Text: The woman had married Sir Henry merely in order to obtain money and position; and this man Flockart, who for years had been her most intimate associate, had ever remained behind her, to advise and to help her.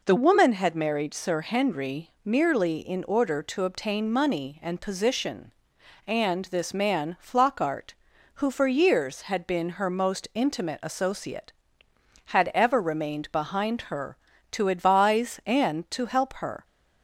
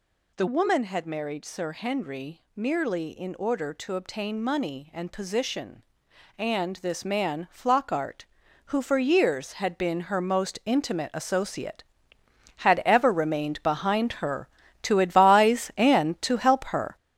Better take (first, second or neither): first